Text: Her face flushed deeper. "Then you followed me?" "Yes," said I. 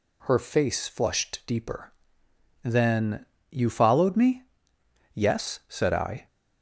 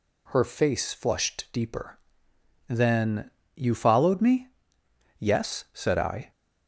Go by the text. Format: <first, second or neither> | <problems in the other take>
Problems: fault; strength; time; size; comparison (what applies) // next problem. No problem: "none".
neither | pauses between "Then" and "you"; slight; the same in both